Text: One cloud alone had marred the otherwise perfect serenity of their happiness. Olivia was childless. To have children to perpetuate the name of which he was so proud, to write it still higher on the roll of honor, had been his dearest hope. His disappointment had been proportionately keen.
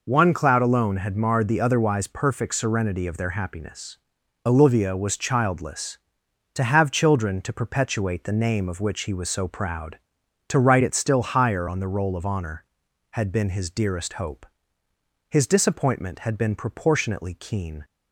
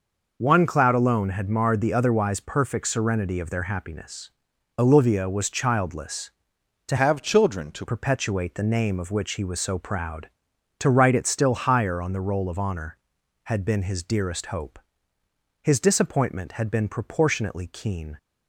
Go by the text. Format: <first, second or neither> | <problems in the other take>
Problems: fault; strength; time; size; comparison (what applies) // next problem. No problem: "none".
first | changes voice from "have" to "to"; from 6.9 to 7.8 s; 0.9 s long